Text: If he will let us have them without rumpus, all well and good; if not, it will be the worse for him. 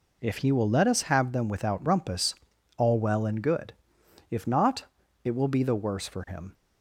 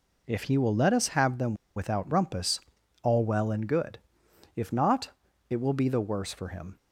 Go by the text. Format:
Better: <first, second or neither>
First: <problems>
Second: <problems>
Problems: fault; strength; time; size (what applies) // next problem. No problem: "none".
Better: first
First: none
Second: pauses between "them" and "without"; slight; at 1.5 s; 0.21 s long